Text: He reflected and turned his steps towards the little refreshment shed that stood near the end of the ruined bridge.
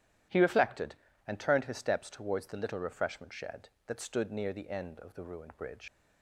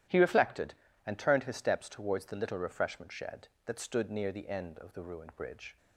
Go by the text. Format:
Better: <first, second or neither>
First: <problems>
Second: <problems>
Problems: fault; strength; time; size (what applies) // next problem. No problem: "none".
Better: second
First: starts louder than the rest; strong; until 1.6 s; 12 dB // leaves "bridge" unfinished; at 5.8 s; 95 ms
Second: starts louder than the rest; strong; until 1.4 s; 12 dB